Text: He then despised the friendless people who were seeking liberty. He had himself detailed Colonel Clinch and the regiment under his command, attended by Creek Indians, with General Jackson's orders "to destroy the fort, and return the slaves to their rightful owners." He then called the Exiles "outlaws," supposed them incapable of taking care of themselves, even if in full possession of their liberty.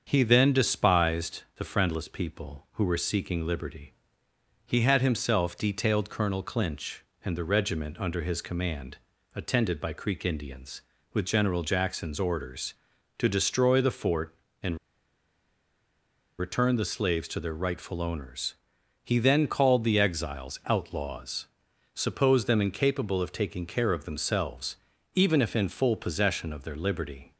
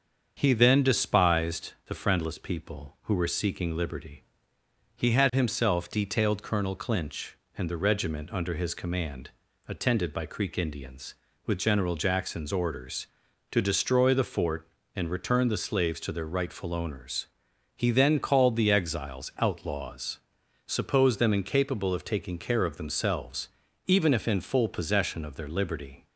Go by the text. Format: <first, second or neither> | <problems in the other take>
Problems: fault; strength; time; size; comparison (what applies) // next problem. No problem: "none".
second | starts louder than the rest; until 1.0 s; 7 dB; also in the second // pauses between "despised" and "the"; slight; at 1.4 s; 0.16 s long; slight in the second // pauses between "and" and "return"; strong; at 14.7 s; 1.6 s long